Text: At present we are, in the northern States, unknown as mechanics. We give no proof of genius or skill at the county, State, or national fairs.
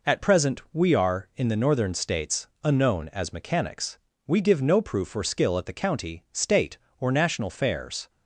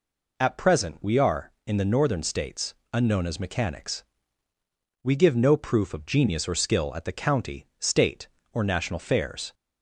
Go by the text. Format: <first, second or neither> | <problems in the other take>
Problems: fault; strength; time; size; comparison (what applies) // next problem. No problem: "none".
second | skips "of genius"; at 5.1 s